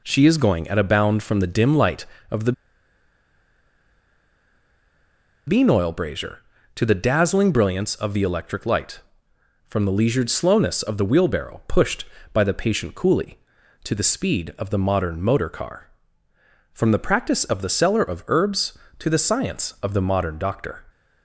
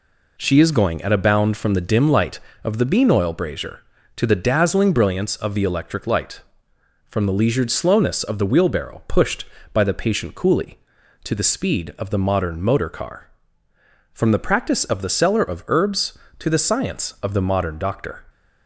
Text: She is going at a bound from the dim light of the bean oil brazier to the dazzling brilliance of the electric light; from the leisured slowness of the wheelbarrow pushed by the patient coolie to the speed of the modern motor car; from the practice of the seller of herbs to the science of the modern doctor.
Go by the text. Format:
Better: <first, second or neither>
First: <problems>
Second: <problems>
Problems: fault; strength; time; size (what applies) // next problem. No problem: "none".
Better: second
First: pauses between "the" and "bean"; strong; at 2.5 s; 2.9 s long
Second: none